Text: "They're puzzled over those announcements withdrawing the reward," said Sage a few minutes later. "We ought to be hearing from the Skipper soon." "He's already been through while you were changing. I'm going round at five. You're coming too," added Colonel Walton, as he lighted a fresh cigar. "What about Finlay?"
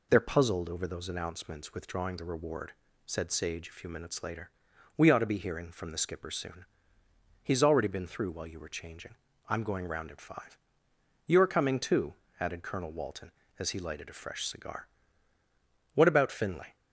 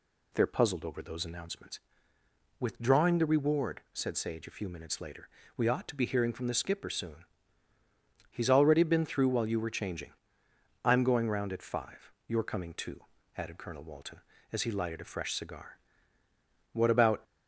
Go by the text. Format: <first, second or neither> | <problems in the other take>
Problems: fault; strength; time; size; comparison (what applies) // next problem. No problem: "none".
first | pauses between "announcements" and "withdrawing"; noticeable; at 1.7 s; 0.80 s long // stops before "Finlay"; at 17.2 s